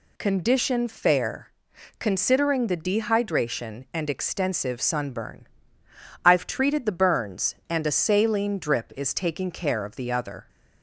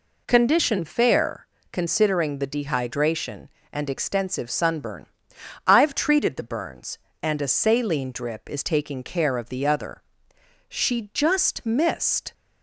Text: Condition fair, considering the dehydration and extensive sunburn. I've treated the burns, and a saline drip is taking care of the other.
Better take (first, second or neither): first